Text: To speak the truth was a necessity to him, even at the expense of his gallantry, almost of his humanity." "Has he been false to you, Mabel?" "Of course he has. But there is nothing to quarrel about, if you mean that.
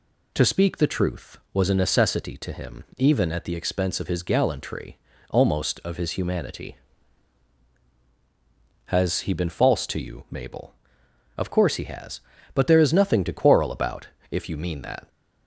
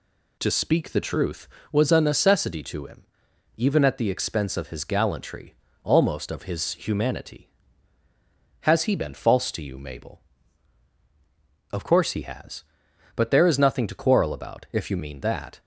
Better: neither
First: none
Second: none

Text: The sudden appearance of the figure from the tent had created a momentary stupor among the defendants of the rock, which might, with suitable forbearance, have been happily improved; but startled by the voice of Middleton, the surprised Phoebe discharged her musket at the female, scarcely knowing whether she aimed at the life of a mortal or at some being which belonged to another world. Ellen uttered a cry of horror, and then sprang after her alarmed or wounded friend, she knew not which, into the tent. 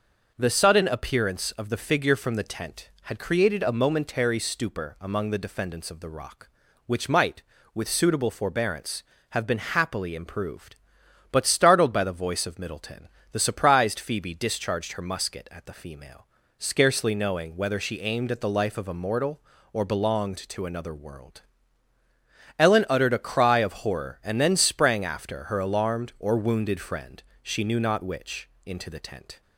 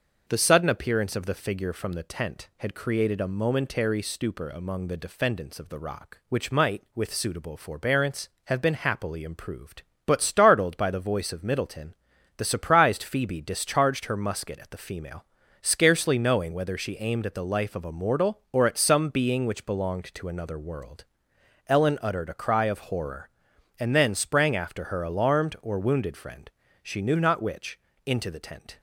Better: second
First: starts louder than the rest; noticeable; until 1.3 s; 6 dB // skips "at some being which"; at 19.8 s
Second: starts louder than the rest; until 1.2 s; 6 dB

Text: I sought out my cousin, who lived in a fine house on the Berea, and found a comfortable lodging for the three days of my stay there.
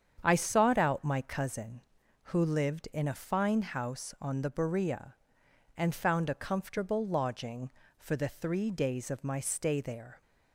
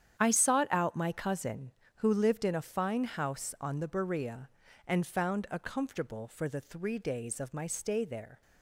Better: first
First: starts louder than the rest; strong; until 1.2 s; 8 dB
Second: starts louder than the rest; strong; until 1.2 s; 9 dB // skips "lodging"; at 6.2 s

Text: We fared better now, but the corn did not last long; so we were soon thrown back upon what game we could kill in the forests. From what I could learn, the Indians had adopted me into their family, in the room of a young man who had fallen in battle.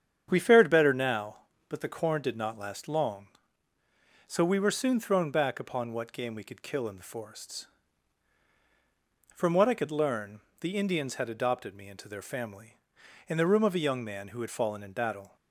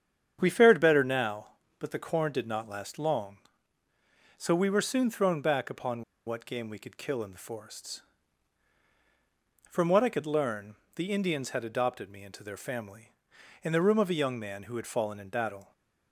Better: first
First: starts louder than the rest; strong; until 1.3 s; 8.5 dB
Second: starts louder than the rest; strong; until 1.4 s; 8.5 dB // pauses between "upon" and "what"; slight; at 6.0 s; 0.24 s long

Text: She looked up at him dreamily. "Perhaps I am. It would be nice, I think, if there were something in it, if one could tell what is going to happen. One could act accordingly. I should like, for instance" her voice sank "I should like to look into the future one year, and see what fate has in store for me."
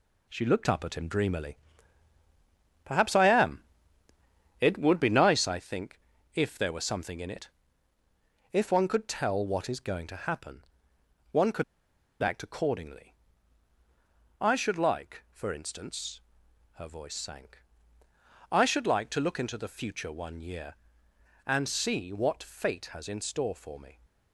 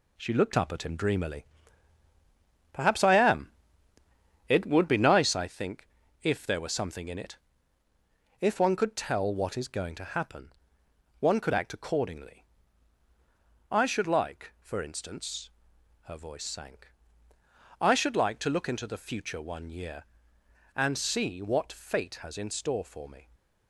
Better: second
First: pauses between "could" and "act"; noticeable; at 11.6 s; 0.57 s long // pauses between "instance" and "her"; noticeable; at 16.1 s; 0.54 s long // pauses between "sank" and "I"; noticeable; at 17.6 s; 0.90 s long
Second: pauses between "instance" and "her"; noticeable; at 15.4 s; 0.54 s long // pauses between "sank" and "I"; noticeable; at 16.9 s; 0.90 s long

